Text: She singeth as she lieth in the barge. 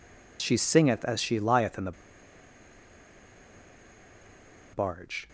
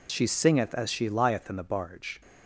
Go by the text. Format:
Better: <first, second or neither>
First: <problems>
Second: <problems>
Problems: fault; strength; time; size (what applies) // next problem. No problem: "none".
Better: second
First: pauses between "the" and "barge"; strong; at 1.9 s; 2.8 s long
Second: none